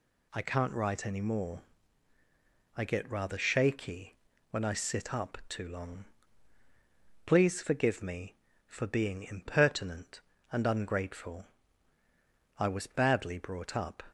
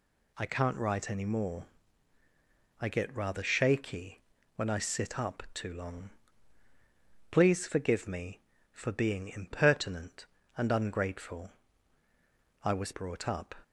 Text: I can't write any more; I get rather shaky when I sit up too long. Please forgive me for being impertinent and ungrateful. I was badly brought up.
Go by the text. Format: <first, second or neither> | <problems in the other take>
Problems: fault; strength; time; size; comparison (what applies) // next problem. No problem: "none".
first | pauses between "shaky" and "when"; slight; at 4.2 s; 0.32 s long; slight in the first // skips "badly"; at 12.9 s